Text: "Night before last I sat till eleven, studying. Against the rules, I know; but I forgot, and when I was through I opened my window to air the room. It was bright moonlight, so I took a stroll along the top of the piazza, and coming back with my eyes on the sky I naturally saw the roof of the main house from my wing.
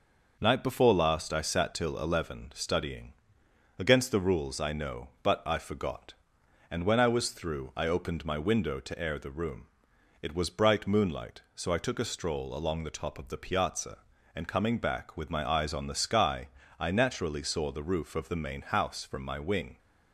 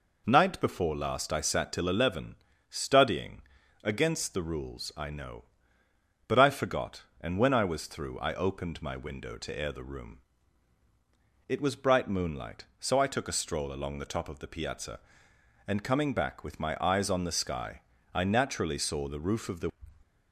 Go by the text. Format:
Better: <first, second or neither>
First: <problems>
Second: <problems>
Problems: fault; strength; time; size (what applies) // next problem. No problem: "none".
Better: first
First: pauses between "sky" and "I"; slight; at 16.4 s; 0.28 s long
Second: pauses between "sky" and "I"; slight; at 17.8 s; 0.30 s long // stops before "main house from my wing"; at 20.0 s